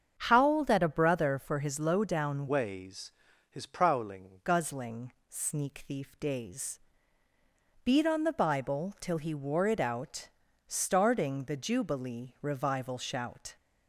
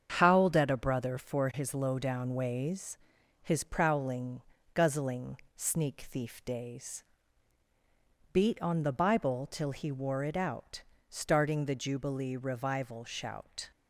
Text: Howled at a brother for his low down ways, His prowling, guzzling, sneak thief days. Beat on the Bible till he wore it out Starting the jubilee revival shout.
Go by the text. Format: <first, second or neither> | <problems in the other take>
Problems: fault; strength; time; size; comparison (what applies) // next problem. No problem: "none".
second | starts louder than the rest; strong; until 1.1 s; 7.5 dB; strong in the second // changes voice from "ways" to "prowling"; from 2.4 to 4.4 s; 2.0 s long // pauses between "out" and "Starting"; slight; at 10.2 s; 0.36 s long; slight in the second